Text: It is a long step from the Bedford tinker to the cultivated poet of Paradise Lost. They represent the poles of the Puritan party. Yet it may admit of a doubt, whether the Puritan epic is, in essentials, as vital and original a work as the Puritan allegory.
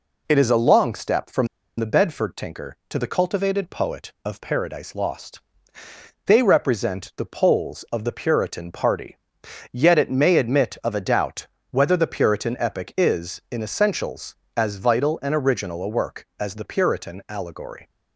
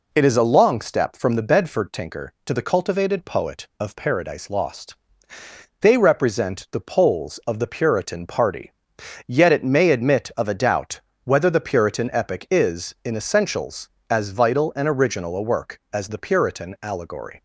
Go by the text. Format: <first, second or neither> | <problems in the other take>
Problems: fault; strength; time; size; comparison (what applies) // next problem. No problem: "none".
second | pauses between "from" and "the"; slight; at 1.4 s; 0.31 s long